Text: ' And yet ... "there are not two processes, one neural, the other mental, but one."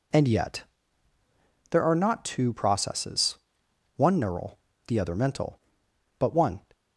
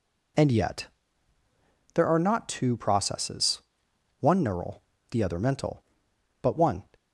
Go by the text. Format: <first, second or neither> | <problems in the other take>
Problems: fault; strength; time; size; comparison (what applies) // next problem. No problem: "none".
neither | none